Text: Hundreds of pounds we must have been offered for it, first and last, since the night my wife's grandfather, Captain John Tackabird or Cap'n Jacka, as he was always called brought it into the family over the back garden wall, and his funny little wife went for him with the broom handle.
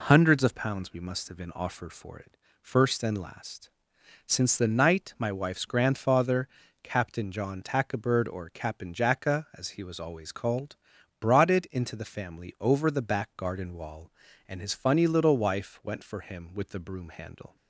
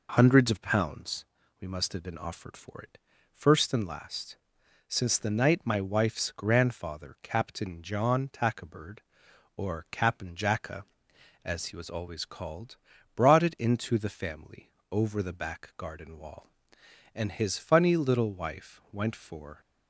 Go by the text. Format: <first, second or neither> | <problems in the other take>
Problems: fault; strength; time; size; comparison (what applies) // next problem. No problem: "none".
first | pauses between "pounds" and "we"; slight; at 1.2 s; 0.36 s long // pauses between "called" and "brought"; at 12.7 s; 0.40 s long; also in the first // pauses between "family" and "over"; slight; at 14.7 s; 0.18 s long // stops before "him with the broom handle"; at 19.6 s